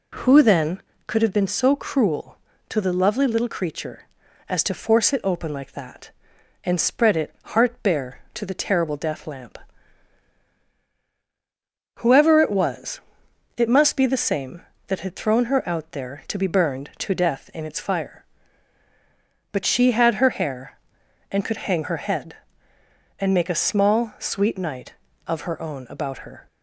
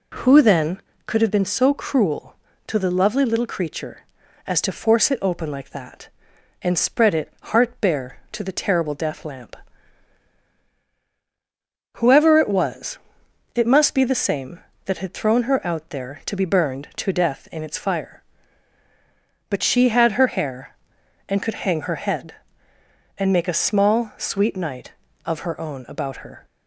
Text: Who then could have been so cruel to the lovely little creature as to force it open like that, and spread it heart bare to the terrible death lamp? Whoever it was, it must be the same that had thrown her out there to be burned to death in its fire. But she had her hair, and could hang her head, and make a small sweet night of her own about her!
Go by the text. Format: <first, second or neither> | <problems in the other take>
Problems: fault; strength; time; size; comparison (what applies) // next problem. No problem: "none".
neither | none